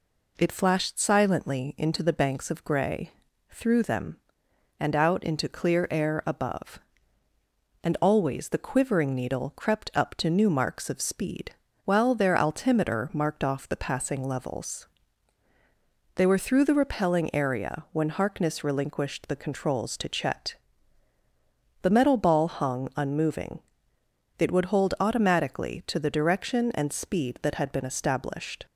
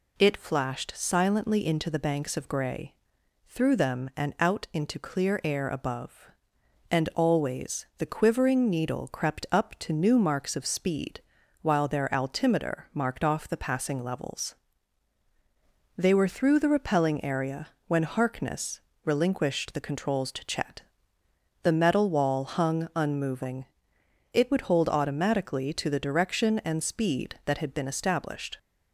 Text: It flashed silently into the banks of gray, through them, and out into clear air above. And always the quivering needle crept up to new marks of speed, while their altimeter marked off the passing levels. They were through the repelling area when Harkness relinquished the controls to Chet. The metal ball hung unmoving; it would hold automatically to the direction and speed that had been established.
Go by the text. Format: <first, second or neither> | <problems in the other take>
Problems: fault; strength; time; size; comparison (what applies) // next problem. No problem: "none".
first | pauses between "area" and "when"; slight; at 17.6 s; 0.20 s long // pauses between "Harkness" and "relinquished"; slight; at 18.7 s; 0.24 s long // says "wall" for "ball"; at 22.0 s